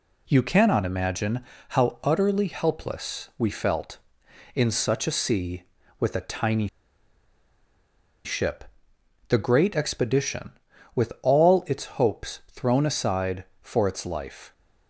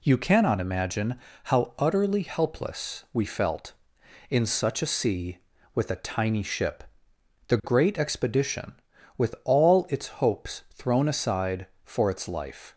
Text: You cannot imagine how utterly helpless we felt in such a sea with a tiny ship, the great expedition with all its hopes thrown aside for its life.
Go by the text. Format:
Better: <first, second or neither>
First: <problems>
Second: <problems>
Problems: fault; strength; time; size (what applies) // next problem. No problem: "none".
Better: second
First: pauses between "imagine" and "how"; slight; at 1.4 s; 0.26 s long // pauses between "tiny" and "ship"; strong; at 6.6 s; 1.5 s long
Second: pauses between "imagine" and "how"; slight; at 1.1 s; 0.26 s long